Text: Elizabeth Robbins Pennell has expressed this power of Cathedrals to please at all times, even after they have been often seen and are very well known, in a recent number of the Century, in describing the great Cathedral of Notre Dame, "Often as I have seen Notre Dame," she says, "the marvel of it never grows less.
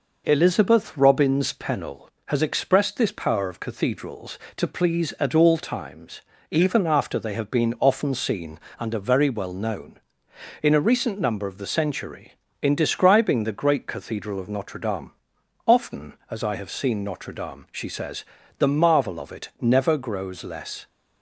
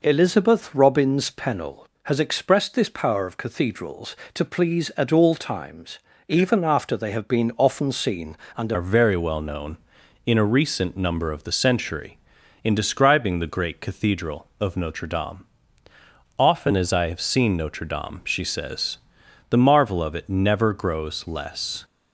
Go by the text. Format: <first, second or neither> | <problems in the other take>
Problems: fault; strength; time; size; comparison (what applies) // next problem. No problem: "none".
first | changes voice at "are"; from 8.7 s on; 13.1 s long